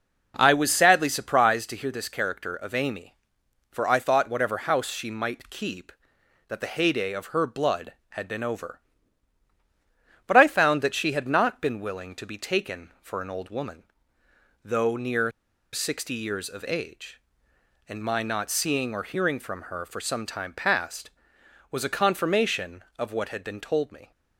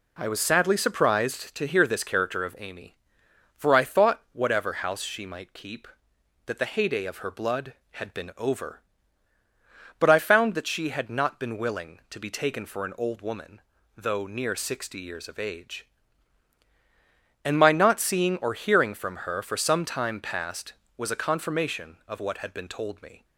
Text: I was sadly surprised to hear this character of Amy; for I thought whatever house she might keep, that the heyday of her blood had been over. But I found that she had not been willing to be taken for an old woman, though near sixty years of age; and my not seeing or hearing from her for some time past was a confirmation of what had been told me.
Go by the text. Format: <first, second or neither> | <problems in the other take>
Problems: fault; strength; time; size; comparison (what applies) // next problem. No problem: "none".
second | pauses between "near" and "sixty"; at 15.3 s; 0.41 s long